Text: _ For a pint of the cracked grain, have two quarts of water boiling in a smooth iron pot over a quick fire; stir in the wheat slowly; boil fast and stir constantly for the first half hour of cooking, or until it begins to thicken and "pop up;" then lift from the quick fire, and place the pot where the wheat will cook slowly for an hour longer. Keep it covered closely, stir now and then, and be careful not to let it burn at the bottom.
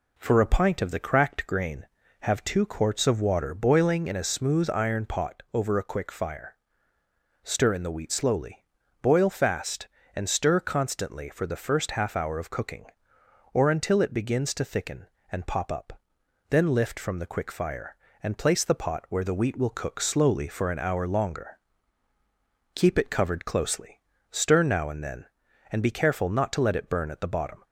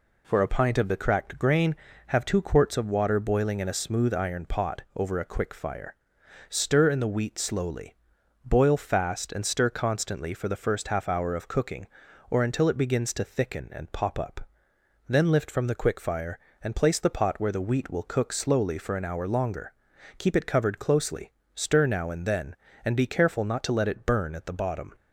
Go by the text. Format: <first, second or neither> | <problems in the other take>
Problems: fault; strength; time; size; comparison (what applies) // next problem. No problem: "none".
neither | none